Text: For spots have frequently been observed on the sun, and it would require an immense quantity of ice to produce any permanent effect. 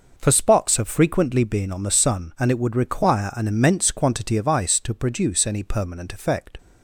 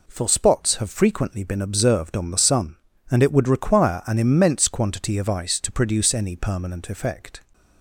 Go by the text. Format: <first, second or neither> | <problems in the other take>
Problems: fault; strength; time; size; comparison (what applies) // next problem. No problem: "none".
second | skips "observed"; at 1.7 s